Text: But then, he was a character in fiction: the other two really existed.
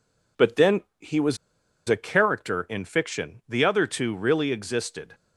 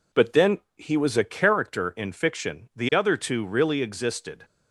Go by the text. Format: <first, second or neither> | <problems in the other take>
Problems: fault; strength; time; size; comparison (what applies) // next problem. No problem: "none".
second | pauses between "was" and "a"; noticeable; at 1.3 s; 0.51 s long